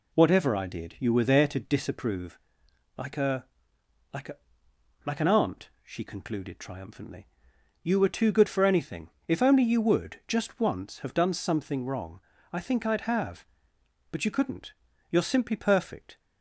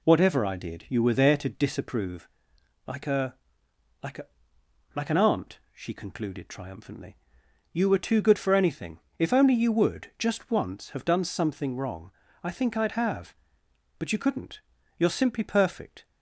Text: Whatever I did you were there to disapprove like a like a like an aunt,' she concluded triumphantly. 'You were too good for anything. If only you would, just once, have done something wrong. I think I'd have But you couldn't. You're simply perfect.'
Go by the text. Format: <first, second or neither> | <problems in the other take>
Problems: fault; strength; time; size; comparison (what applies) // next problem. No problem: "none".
neither | pauses between "disapprove" and "like"; noticeable; the same in both // pauses between "a" and "like"; noticeable; the same in both // pauses between "a" and "like"; noticeable; the same in both